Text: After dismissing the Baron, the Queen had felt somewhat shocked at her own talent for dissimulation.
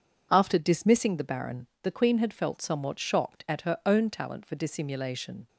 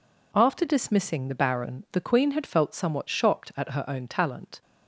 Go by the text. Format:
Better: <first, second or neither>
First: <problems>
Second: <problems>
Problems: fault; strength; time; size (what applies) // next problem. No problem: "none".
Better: first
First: none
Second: stops before "for dissimulation"; at 4.6 s